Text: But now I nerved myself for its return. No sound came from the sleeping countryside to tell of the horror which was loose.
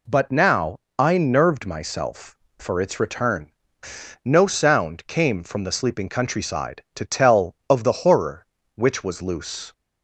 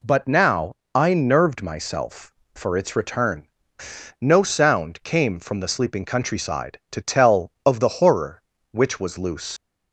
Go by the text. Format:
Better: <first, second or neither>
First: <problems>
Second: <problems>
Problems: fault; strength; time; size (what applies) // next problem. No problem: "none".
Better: first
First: pauses between "now" and "I"; slight; at 0.7 s; 0.22 s long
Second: pauses between "now" and "I"; slight; at 0.7 s; 0.22 s long // leaves "loose" unfinished; at 9.5 s; 120 ms